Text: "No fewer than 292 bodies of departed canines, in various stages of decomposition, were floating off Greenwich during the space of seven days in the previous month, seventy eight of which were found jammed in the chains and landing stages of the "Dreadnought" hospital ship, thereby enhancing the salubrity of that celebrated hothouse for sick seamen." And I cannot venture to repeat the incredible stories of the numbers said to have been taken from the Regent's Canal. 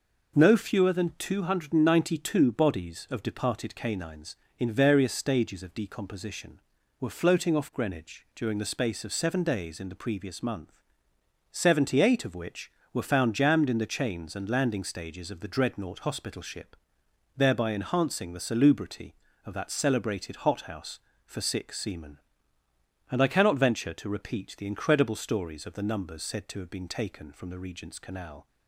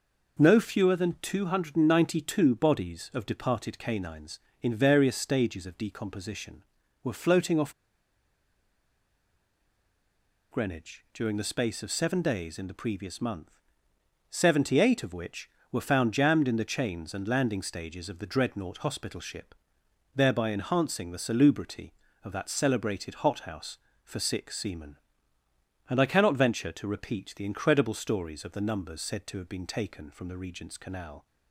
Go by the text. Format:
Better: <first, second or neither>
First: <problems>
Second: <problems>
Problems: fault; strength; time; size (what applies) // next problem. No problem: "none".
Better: first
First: none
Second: pauses between "off" and "Greenwich"; strong; at 7.7 s; 2.7 s long